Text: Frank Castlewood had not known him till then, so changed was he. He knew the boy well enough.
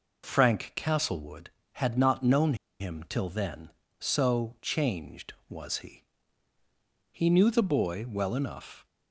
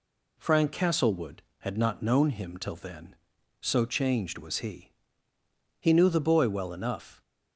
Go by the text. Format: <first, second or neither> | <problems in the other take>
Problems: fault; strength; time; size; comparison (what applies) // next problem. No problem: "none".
second | pauses between "known" and "him"; slight; at 2.5 s; 0.25 s long